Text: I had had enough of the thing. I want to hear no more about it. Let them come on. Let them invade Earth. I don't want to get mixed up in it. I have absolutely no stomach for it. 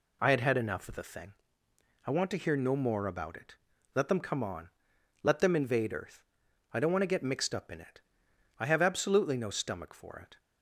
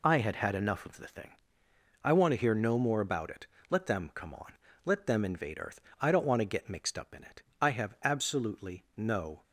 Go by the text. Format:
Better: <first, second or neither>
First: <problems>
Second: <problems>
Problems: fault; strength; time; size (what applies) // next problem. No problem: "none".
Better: first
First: none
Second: stops before "stomach for it"; at 9.4 s